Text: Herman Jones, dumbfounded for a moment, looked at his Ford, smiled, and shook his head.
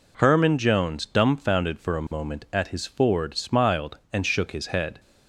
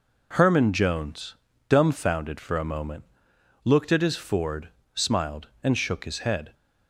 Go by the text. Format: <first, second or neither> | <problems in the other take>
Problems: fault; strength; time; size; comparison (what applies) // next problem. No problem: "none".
second | skips "looked"; at 2.4 s